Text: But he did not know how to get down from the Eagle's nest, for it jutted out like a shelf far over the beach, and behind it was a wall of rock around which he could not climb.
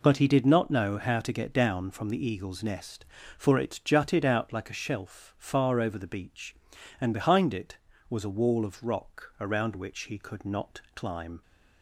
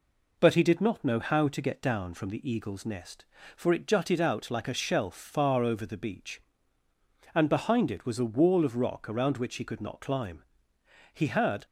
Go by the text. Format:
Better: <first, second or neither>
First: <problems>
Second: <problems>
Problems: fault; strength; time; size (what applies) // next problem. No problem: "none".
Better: first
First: none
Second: goes on to say "He had"; from 11.1 s on; 0.52 s long